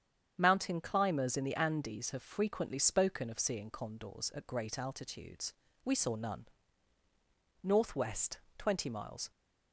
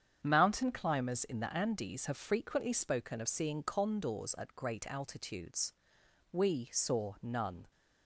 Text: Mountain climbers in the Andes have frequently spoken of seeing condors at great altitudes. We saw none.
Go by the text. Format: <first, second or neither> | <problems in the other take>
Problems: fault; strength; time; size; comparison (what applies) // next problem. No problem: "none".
second | starts louder than the rest; strong; until 1.3 s; 8.5 dB; strong in the second // goes on to say "Northwest twenty miles"; strong; from 7.6 s on; 1.7 s long